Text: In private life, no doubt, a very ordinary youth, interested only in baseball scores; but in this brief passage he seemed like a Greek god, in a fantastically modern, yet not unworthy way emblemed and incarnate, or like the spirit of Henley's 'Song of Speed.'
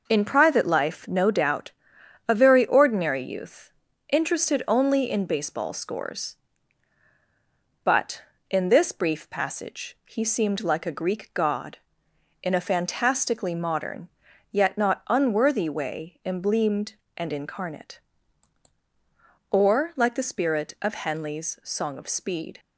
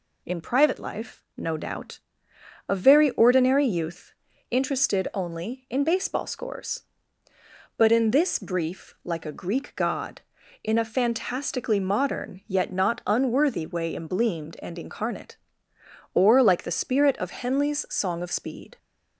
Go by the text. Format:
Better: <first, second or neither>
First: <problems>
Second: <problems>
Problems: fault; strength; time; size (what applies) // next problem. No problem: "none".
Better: first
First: none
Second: skips "passage he seemed"; at 8.9 s